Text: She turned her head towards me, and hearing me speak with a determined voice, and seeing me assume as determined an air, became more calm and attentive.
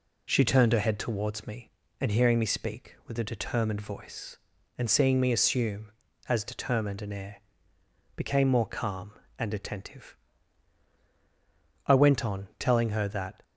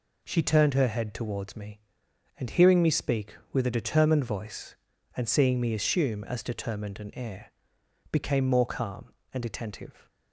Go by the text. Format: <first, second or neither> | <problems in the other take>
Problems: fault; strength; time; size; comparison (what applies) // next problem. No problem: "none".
second | goes on to say "I went on telling her that"; from 11.8 s on; 1.5 s long